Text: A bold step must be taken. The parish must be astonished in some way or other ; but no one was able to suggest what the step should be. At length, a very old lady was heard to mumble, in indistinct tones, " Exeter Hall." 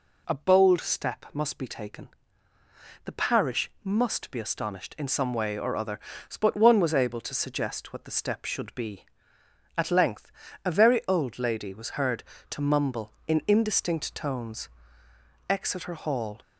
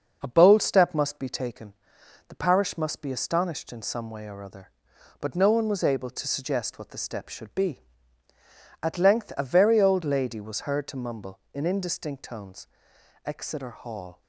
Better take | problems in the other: second | skips "no"; at 6.5 s

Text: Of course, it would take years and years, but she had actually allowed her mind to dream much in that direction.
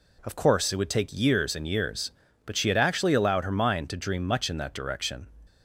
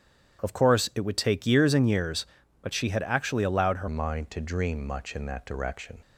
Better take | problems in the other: first | starts louder than the rest; strong; until 1.4 s; 9.5 dB // changes voice at "mind"; from 3.8 s on; 2.1 s long

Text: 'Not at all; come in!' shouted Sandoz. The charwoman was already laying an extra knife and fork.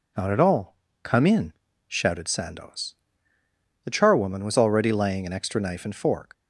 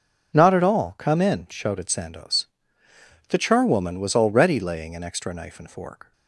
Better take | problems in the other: neither | none

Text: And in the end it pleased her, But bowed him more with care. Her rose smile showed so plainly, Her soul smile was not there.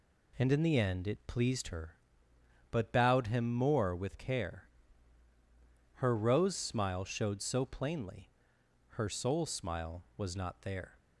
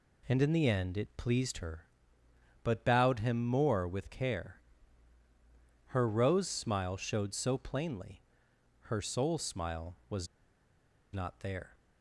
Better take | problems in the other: first | pauses between "was" and "not"; noticeable; at 10.2 s; 0.87 s long

